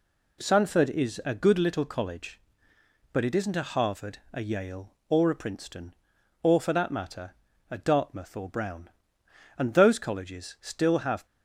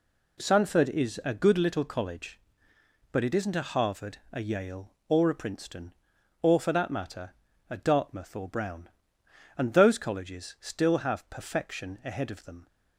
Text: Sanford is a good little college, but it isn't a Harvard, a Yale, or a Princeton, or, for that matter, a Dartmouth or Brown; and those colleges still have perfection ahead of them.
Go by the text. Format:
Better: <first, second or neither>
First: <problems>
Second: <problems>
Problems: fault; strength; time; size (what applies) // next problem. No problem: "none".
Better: second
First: stops before "perfection ahead of them"; at 11.2 s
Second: none